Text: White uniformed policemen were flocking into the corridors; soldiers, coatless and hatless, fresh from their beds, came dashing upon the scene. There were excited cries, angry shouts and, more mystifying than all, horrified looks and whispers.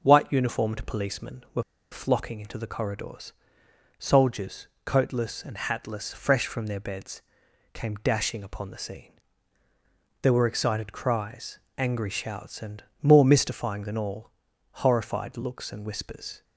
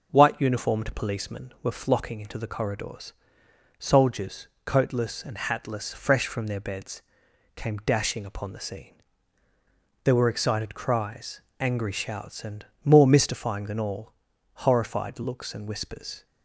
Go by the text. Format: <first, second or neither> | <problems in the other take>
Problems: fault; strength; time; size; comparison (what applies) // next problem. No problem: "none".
second | pauses between "were" and "flocking"; slight; at 1.6 s; 0.30 s long